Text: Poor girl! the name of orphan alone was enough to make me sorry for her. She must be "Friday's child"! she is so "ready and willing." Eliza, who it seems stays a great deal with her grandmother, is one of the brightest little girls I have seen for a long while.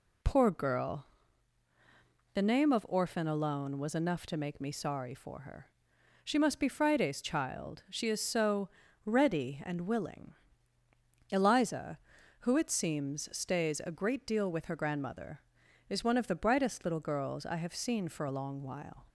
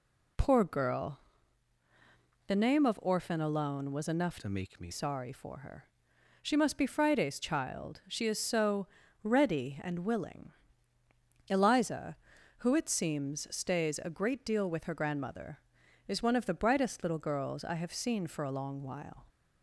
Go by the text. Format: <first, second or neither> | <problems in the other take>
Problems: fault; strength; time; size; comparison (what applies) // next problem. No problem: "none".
first | changes voice from "to" to "me"; from 4.3 to 4.9 s; 0.6 s long // pauses between "so" and "ready"; slight; at 8.8 s; 0.34 s long; slight in the first